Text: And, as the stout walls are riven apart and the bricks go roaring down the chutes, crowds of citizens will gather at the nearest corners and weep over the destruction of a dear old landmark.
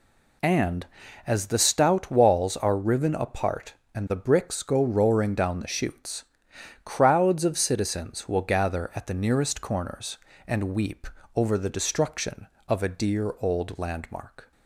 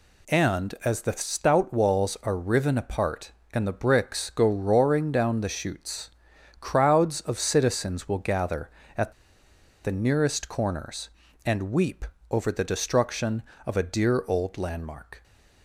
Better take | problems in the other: first | pauses between "at" and "the"; noticeable; at 9.1 s; 0.72 s long // pauses between "weep" and "over"; slight; at 12.0 s; 0.26 s long; slight in the first

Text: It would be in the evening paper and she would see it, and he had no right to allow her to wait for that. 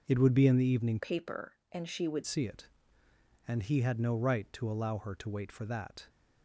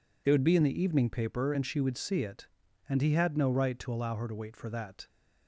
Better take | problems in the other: second | changes voice from "paper" to "would"; from 0.9 to 2.2 s; 1.3 s long

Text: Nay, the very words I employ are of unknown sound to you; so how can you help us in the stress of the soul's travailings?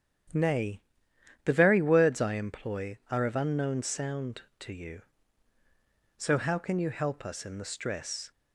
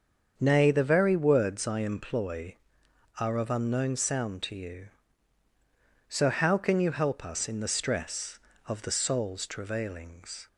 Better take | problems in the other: second | starts louder than the rest; strong; until 1.9 s; 9 dB; also in the second // stops before "of the soul's travailings"; at 8.3 s

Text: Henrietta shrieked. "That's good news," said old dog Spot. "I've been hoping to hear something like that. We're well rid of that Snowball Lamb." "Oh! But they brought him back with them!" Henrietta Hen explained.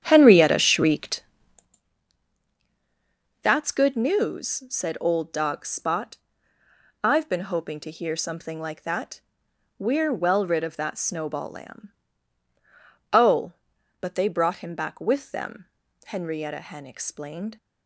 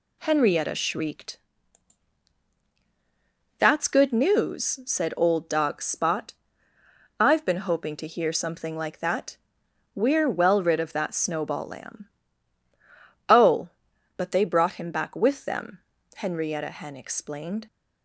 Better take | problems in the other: second | starts louder than the rest; strong; until 1.8 s; 9.5 dB

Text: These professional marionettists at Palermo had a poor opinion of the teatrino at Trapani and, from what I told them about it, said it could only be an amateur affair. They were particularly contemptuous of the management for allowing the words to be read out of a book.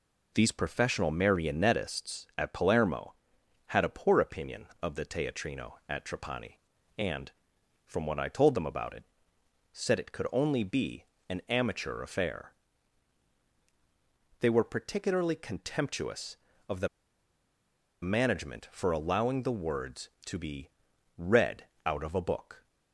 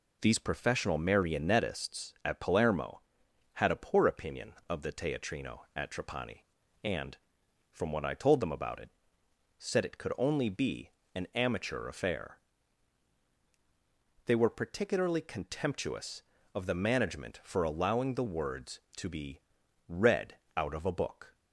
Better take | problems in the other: second | pauses between "be" and "an"; slight; at 11.0 s; 0.24 s long; slight in the second // pauses between "the" and "management"; at 16.8 s; 1.1 s long // pauses between "be" and "read"; noticeable; at 20.7 s; 0.46 s long; noticeable in the second // pauses between "read" and "out"; slight; at 21.6 s; 0.18 s long; slight in the second

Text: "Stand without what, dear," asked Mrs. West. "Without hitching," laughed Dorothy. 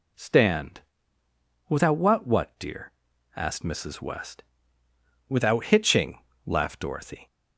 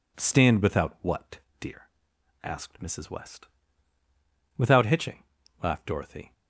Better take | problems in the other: second | pauses between "Stand" and "without"; noticeable; at 0.8 s; 0.88 s long // says "what" twice; at 2.2 s

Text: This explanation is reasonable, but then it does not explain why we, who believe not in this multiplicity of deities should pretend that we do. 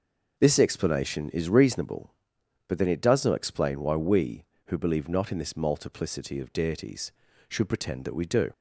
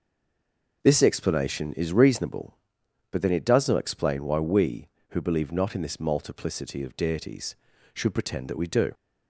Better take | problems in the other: first | stays silent before the first word; slight; until 0.8 s; 0.8 s long

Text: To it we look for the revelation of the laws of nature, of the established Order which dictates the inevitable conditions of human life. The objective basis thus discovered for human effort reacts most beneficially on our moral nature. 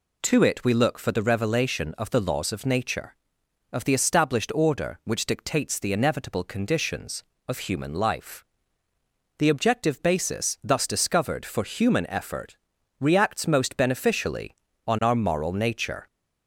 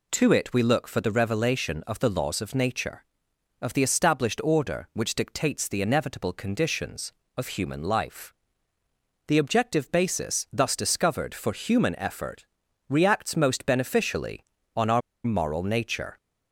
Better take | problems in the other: first | pauses between "effort" and "reacts"; at 12.4 s; 0.42 s long; also in the first // pauses between "our" and "moral"; slight; at 15.0 s; 0.25 s long

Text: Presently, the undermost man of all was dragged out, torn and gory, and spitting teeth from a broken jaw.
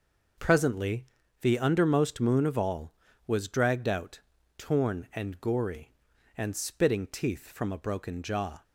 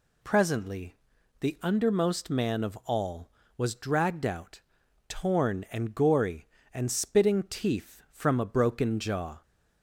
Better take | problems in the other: second | says "moon" for "man"; at 2.2 s

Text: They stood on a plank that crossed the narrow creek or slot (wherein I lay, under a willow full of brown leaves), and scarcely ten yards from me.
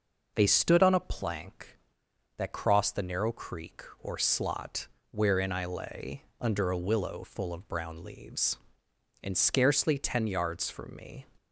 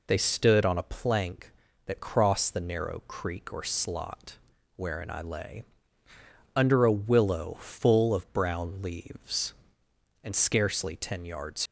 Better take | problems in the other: first | stops before "from me"; at 11.6 s

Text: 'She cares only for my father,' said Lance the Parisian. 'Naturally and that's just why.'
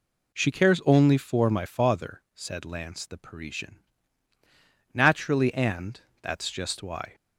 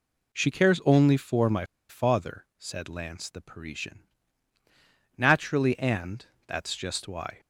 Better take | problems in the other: first | pauses between "my" and "father"; slight; at 1.6 s; 0.24 s long // pauses between "and" and "that's"; slight; at 6.2 s; 0.22 s long; slight in the first

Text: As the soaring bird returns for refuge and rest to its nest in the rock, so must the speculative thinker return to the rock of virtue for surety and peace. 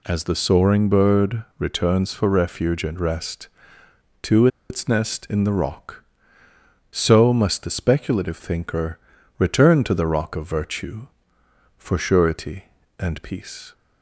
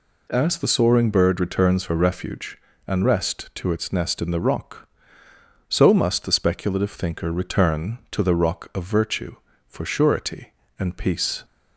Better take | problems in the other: second | pauses between "bird" and "returns"; slight; at 1.4 s; 0.16 s long // pauses between "to" and "its"; slight; at 4.4 s; 0.22 s long // pauses between "thinker" and "return"; at 8.9 s; 0.40 s long

